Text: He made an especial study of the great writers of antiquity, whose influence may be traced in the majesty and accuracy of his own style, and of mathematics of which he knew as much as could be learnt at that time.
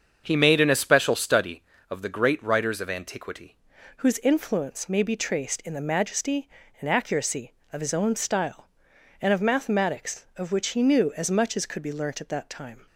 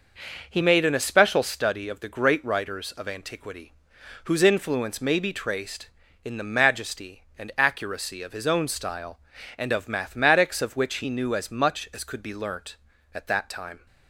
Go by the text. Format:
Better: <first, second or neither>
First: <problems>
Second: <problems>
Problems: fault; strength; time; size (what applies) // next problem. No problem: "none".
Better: second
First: starts louder than the rest; until 1.2 s; 7 dB // changes voice at "whose"; from 3.9 s on; 8.9 s long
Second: none